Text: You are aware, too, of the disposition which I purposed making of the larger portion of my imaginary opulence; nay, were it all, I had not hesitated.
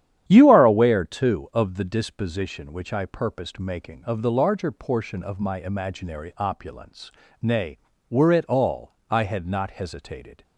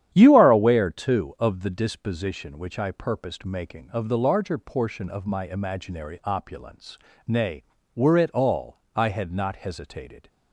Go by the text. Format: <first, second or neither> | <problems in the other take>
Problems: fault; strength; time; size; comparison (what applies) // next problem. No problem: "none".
neither | starts louder than the rest; strong; the same in both